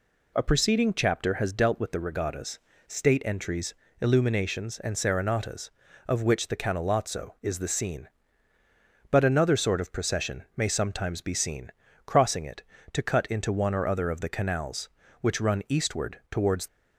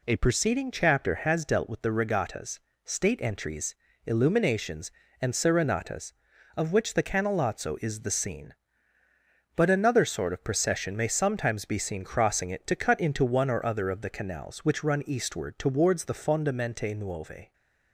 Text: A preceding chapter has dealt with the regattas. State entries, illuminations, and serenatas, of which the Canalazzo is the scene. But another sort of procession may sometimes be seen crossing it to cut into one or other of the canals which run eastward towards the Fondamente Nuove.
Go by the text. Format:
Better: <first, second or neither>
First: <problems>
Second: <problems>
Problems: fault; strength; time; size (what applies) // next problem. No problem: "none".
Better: second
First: pauses between "seen" and "crossing"; slight; at 11.7 s; 0.34 s long // stops before "the Fondamente Nuove"; at 16.6 s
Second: none